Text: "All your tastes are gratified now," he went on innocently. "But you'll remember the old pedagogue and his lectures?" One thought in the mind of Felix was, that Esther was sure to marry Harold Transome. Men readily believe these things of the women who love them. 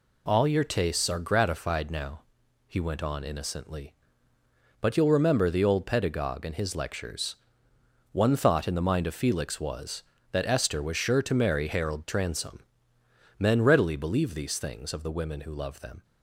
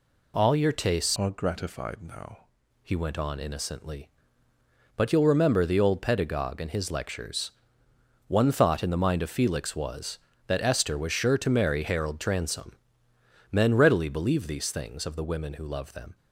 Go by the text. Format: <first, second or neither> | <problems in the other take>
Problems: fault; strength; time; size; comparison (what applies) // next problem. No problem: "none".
first | changes voice from "are" to "now"; from 1.1 to 2.4 s; 1.3 s long